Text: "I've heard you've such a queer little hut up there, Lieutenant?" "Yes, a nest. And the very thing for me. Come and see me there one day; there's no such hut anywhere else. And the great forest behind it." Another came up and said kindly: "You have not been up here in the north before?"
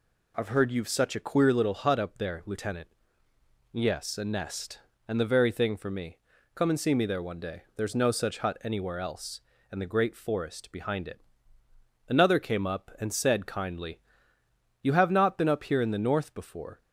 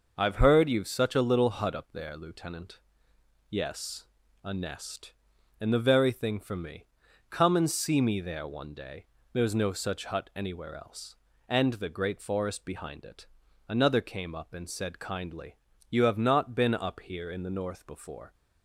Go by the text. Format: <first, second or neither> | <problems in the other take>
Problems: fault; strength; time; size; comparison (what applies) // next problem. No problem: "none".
first | skips "queer"; at 1.2 s